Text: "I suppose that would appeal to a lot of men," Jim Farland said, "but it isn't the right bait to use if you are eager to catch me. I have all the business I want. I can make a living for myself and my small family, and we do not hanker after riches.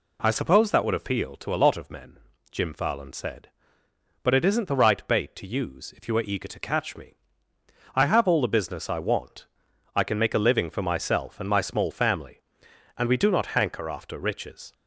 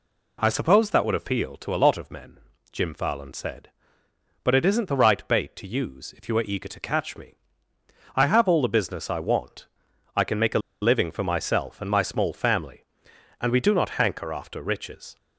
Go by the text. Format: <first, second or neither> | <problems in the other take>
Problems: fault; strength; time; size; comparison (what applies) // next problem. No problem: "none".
first | pauses between "a" and "living"; slight; at 10.5 s; 0.22 s long